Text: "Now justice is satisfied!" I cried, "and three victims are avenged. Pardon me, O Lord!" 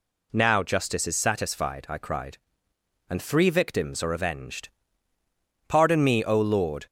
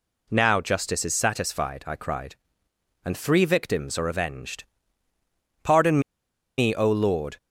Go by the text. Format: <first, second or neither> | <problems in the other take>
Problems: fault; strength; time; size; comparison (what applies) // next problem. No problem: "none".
first | pauses between "Pardon" and "me"; noticeable; at 5.9 s; 0.58 s long